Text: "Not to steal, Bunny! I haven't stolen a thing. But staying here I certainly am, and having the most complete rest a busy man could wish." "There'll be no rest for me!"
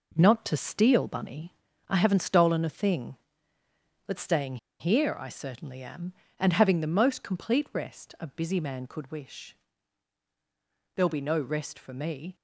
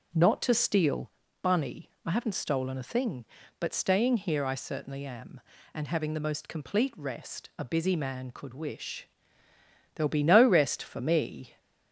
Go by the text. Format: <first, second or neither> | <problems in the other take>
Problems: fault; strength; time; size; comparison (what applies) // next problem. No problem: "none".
second | pauses between "staying" and "here"; slight; at 4.5 s; 0.23 s long